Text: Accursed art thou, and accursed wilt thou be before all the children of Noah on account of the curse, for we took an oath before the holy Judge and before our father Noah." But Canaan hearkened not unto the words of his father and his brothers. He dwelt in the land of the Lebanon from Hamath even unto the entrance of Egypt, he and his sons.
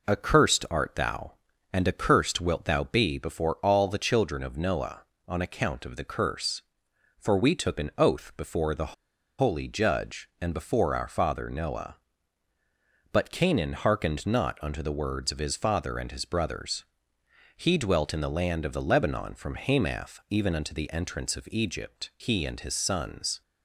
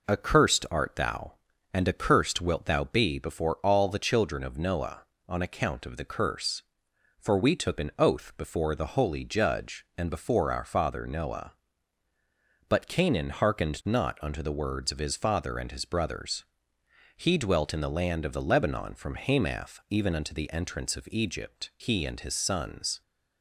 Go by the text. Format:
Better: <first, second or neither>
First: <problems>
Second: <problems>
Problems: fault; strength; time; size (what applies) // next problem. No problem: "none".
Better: second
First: pauses between "the" and "holy"; noticeable; at 8.9 s; 0.46 s long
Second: none